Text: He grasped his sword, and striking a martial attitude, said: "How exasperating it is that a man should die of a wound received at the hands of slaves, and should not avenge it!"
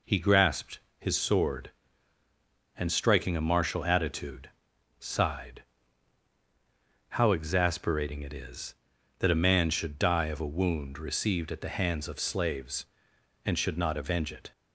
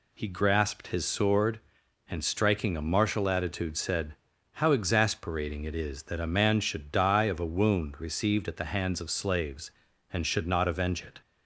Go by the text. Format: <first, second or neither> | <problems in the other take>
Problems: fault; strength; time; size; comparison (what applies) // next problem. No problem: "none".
second | pauses between "grasped" and "his"; slight; at 0.7 s; 0.18 s long // says "sighed" for "said"; at 4.9 s